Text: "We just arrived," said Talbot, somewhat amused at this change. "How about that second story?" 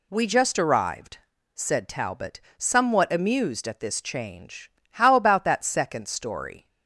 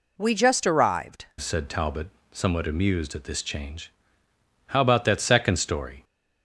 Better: first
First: none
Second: changes voice at "said"; from 1.3 s on; 4.7 s long

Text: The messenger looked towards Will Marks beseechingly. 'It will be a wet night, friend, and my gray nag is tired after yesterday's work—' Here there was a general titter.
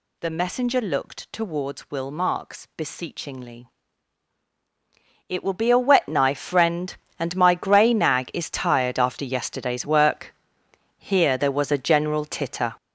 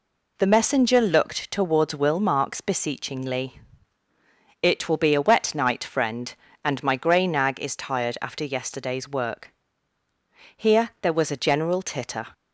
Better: second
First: says "knife" for "night"; at 6.0 s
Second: none

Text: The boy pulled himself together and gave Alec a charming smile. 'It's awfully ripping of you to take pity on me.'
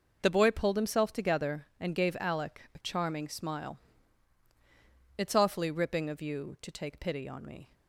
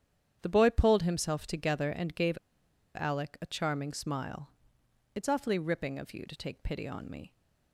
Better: first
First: none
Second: starts louder than the rest; strong; until 1.4 s; 9 dB // pauses between "gave" and "Alec"; noticeable; at 2.3 s; 0.57 s long

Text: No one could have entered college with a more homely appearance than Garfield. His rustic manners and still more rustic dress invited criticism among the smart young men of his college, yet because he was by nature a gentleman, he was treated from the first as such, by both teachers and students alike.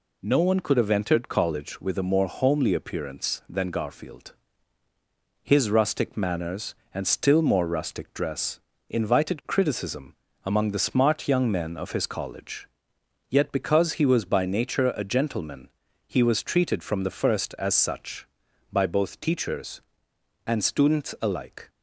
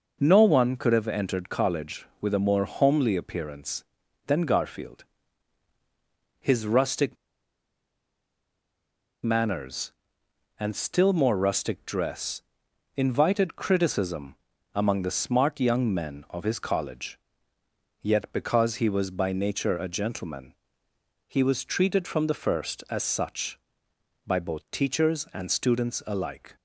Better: first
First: pauses between "dress" and "invited"; slight; at 8.5 s; 0.30 s long // pauses between "criticism" and "among"; slight; at 10.1 s; 0.30 s long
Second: pauses between "rustic" and "manners"; strong; at 7.1 s; 2.0 s long // pauses between "dress" and "invited"; noticeable; at 12.4 s; 0.54 s long // pauses between "criticism" and "among"; at 14.3 s; 0.40 s long

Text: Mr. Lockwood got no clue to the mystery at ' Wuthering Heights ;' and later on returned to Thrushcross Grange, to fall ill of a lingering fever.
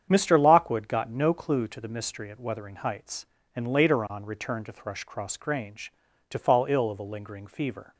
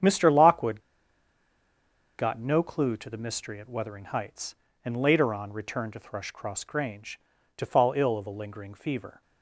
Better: first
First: starts louder than the rest; strong; until 1.1 s; 8.5 dB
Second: starts louder than the rest; strong; until 2.4 s; 8.5 dB // pauses between "Lockwood" and "got"; strong; at 0.8 s; 1.3 s long

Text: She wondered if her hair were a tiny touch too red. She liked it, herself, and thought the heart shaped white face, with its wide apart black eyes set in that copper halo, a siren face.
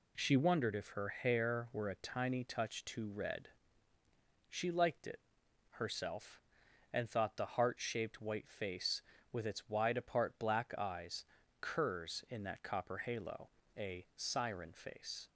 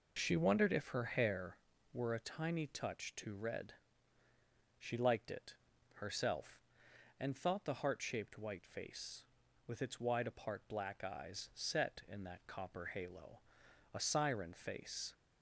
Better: second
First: says "curs" for "set"; at 11.5 s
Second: none

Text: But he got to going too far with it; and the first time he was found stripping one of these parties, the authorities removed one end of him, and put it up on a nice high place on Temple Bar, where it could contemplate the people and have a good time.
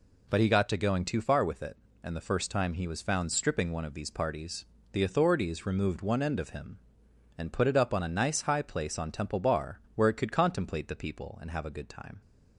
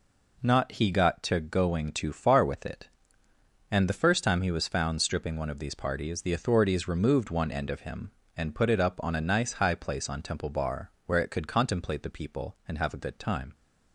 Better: first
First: none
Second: says "Not" for "But"; at 0.4 s

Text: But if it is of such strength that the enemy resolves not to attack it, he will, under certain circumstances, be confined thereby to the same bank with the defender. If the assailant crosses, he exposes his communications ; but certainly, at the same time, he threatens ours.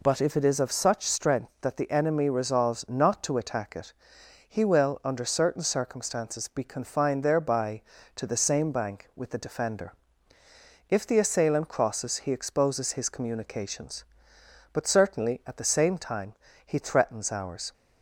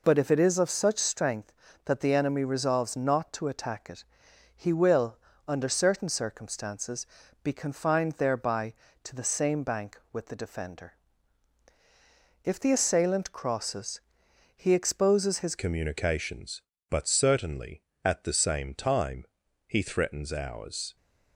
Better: first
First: none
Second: changes voice at "communications"; from 15.5 s on; 5.4 s long

